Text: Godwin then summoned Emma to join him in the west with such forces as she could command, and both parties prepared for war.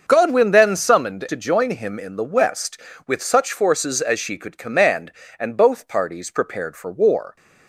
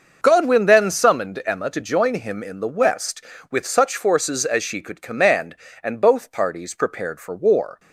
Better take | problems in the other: second | starts louder than the rest; until 1.0 s; 6 dB; also in the second // skips "Emma"; at 1.2 s

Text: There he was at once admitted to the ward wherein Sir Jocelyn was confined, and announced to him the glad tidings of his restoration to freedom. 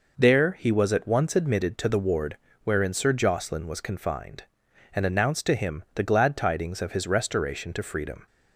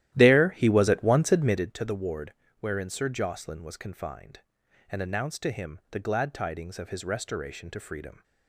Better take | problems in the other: first | starts louder than the rest; strong; until 1.8 s; 13 dB // pauses between "ward" and "wherein"; slight; at 2.3 s; 0.26 s long; slight in the first

